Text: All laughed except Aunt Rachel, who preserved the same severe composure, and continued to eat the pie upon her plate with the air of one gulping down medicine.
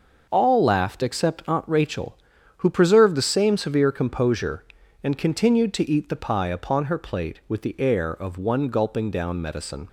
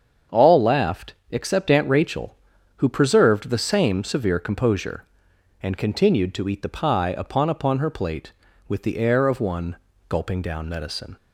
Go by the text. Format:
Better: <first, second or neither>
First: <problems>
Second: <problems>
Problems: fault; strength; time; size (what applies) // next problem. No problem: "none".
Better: first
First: none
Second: starts louder than the rest; strong; until 1.4 s; 7.5 dB // pauses between "laughed" and "except"; slight; at 1.1 s; 0.16 s long // says "upon" twice; at 7.5 s // pauses between "one" and "gulping"; slight; at 9.7 s; 0.32 s long